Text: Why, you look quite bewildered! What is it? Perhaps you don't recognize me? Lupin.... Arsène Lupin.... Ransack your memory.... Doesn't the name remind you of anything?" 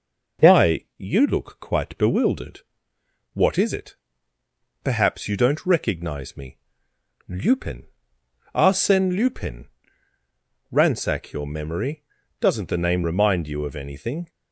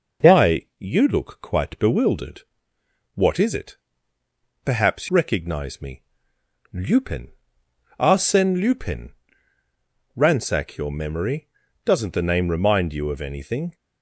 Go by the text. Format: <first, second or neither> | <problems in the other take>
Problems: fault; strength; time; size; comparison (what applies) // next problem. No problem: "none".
first | skips "you don't"; at 5.0 s